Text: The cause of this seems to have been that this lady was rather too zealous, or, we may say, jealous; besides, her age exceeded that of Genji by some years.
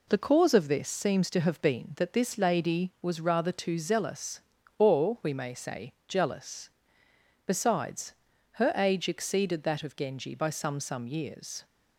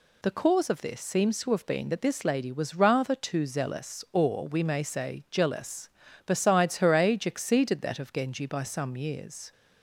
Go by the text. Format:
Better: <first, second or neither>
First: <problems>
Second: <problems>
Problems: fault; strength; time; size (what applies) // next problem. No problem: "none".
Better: second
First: says "some" twice; at 10.8 s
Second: none